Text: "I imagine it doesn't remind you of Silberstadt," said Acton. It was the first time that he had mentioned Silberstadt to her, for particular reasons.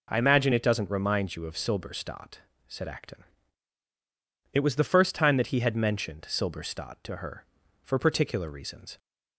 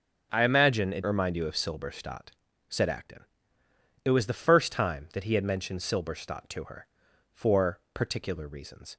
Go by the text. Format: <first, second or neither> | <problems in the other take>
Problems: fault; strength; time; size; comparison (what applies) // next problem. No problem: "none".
first | skips "doesn't"; at 1.0 s